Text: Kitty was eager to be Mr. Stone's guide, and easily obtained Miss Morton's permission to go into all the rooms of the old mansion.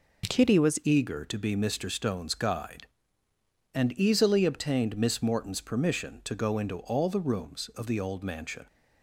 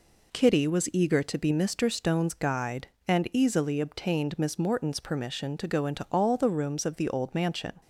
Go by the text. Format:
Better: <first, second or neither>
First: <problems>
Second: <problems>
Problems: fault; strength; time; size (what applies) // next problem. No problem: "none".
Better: second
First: changes voice at "eager"; from 0.8 s on; 7.8 s long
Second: none